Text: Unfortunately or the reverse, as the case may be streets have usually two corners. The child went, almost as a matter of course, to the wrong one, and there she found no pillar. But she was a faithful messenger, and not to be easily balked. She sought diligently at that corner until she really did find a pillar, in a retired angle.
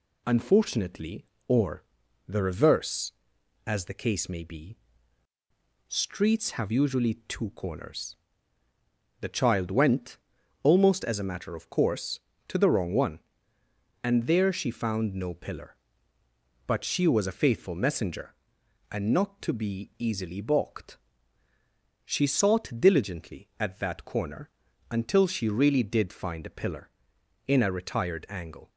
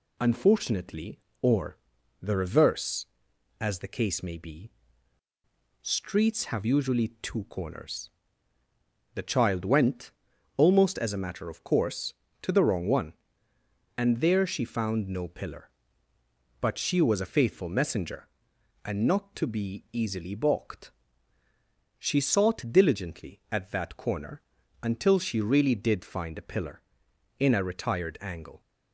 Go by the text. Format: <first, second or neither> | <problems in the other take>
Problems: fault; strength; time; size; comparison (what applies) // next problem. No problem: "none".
neither | pauses between "or" and "the"; the same in both // pauses between "be" and "streets"; the same in both // pauses between "corner" and "until"; the same in both